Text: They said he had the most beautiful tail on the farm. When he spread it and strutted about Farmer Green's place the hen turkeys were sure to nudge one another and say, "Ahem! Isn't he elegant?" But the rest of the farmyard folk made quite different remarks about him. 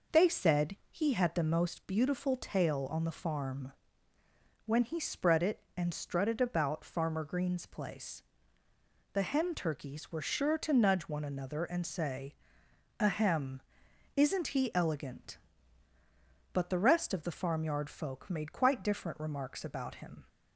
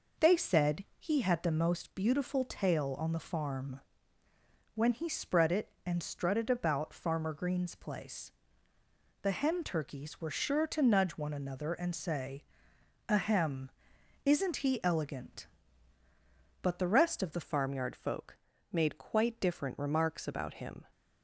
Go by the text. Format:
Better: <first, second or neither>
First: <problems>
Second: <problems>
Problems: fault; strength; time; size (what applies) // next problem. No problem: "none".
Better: first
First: pauses between "said" and "he"; slight; at 0.7 s; 0.16 s long // pauses between "place" and "the"; noticeable; at 8.2 s; 0.92 s long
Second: pauses between "said" and "he"; slight; at 0.8 s; 0.16 s long // pauses between "place" and "the"; noticeable; at 8.3 s; 0.92 s long // changes voice at "farmyard"; from 17.4 s on; 3.4 s long // pauses between "folk" and "made"; slight; at 18.3 s; 0.34 s long